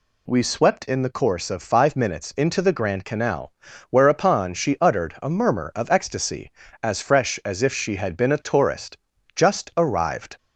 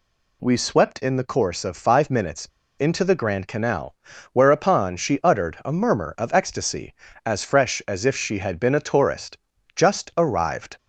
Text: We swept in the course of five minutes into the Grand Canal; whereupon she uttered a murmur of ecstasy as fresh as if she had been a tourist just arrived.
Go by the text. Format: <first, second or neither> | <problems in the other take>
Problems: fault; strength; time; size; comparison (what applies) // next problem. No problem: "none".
first | pauses between "minutes" and "into"; slight; at 2.4 s; 0.32 s long // pauses between "tourist" and "just"; slight; at 9.3 s; 0.36 s long; slight in the first